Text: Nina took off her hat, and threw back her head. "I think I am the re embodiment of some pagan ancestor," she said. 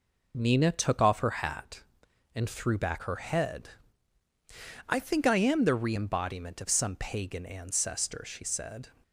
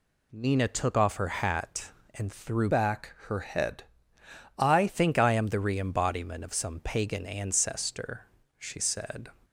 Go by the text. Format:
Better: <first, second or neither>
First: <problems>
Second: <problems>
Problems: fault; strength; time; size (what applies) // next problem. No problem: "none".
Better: first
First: none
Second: changes voice from "back" to "I"; from 2.6 to 4.8 s; 2.2 s long